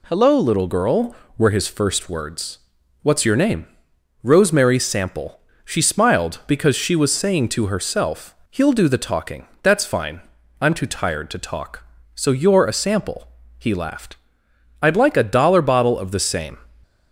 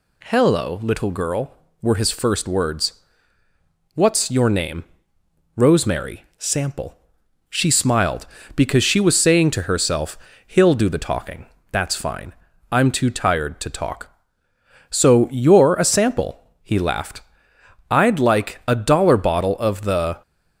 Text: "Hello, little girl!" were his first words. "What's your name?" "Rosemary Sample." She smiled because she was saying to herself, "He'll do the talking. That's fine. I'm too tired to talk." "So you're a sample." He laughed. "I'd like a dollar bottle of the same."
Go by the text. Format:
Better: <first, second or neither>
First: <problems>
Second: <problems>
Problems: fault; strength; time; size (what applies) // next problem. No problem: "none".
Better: first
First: none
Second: stops before "same"; at 20.2 s